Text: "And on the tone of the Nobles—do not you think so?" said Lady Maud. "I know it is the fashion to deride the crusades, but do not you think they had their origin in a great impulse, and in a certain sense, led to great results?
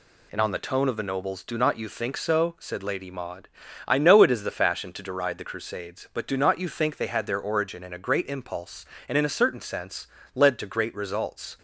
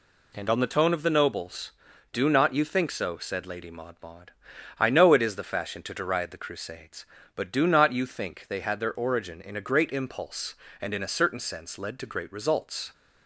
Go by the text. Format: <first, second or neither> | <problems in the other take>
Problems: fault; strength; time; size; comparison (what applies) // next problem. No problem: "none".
first | says "Maud" twice; at 4.0 s